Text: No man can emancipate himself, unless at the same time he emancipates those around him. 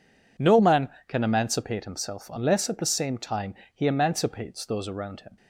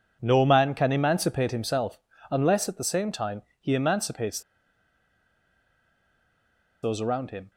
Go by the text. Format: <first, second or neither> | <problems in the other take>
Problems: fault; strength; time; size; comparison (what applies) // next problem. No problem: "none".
first | pauses between "time" and "he"; slight; at 3.4 s; 0.18 s long; slight in the first // pauses between "emancipates" and "those"; strong; at 4.4 s; 2.4 s long